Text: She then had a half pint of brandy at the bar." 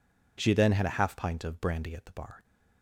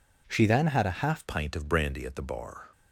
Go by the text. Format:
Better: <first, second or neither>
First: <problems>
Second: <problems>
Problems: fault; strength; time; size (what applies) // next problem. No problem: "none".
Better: first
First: none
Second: changes voice at "pint"; from 1.2 s on; 1.4 s long